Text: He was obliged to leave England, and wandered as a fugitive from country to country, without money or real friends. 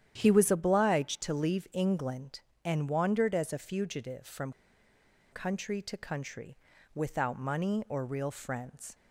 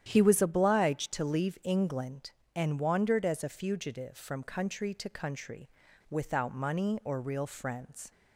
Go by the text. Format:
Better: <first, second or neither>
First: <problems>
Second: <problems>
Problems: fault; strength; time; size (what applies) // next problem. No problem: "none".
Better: second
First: starts louder than the rest; strong; until 1.1 s; 10 dB // pauses between "from" and "country"; noticeable; at 4.5 s; 0.81 s long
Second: starts louder than the rest; strong; until 1.0 s; 10 dB